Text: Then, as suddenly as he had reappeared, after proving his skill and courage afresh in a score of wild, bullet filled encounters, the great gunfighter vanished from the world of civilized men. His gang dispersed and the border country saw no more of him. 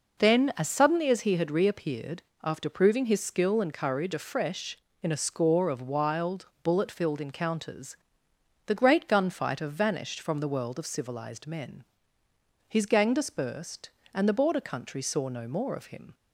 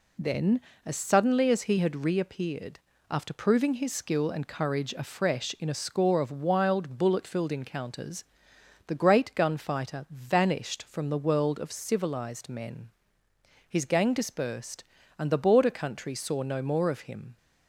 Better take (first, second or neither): neither